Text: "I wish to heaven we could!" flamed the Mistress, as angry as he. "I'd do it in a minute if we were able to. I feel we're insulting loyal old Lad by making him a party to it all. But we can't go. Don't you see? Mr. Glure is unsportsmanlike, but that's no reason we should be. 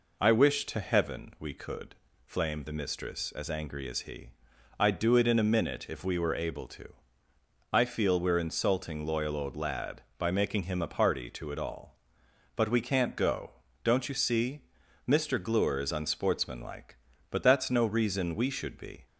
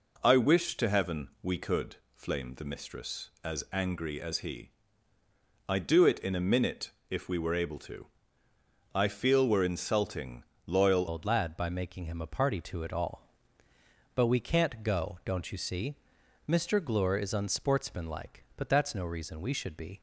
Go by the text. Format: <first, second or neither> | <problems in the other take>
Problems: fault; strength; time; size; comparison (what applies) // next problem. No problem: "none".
first | pauses between "minute" and "if"; slight; at 6.9 s; 0.20 s long // pauses between "insulting" and "loyal"; slight; at 10.4 s; 0.22 s long // changes voice at "old"; from 11.0 s on; 8.9 s long